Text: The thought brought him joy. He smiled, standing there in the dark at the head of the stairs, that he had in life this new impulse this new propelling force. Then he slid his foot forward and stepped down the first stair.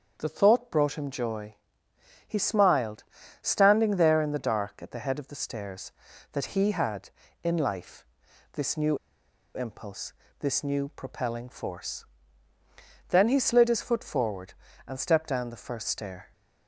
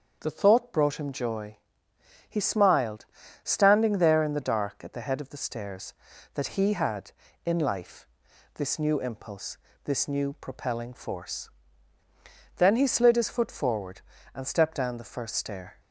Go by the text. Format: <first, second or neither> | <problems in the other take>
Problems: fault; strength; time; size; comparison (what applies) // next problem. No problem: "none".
second | starts louder than the rest; until 1.1 s; 7 dB; also in the second // pauses between "life" and "this"; noticeable; at 8.0 s; 0.48 s long; noticeable in the second // pauses between "new" and "impulse"; noticeable; at 8.9 s; 0.58 s long // pauses between "impulse" and "this"; slight; at 10.1 s; 0.26 s long; slight in the second